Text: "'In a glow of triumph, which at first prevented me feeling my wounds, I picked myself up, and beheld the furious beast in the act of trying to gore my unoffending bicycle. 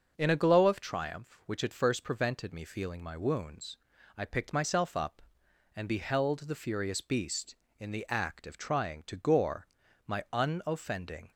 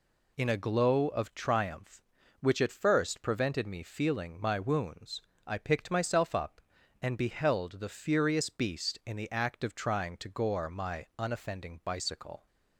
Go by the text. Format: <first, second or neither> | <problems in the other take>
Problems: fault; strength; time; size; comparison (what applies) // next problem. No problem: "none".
second | starts louder than the rest; until 1.1 s; 6.5 dB // pauses between "gore" and "my"; at 9.6 s; 0.40 s long // stops before "bicycle"; at 11.3 s